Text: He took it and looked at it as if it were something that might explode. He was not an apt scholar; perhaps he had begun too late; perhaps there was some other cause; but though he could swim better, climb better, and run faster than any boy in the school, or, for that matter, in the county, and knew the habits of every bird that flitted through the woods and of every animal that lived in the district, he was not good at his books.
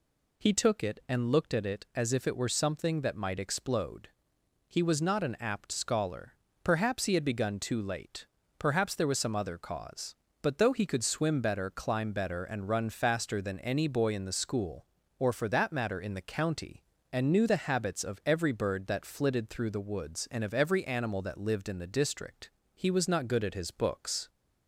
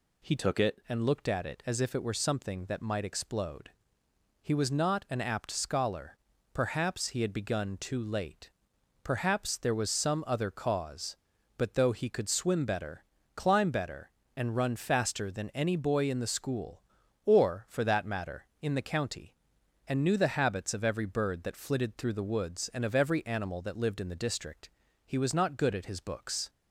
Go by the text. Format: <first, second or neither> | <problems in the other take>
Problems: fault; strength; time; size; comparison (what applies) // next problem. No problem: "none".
first | changes voice from "took" to "it"; from 0.3 to 0.7 s; 0.4 s long